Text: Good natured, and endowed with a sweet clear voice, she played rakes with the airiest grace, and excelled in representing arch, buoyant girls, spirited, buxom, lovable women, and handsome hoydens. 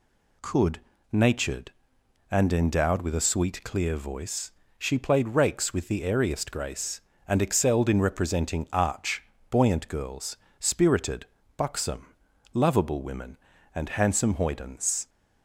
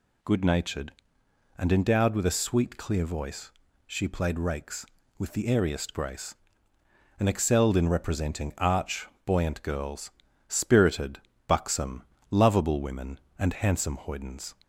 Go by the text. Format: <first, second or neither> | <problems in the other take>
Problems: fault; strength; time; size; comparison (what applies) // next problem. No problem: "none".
second | says "Could" for "Good"; at 0.4 s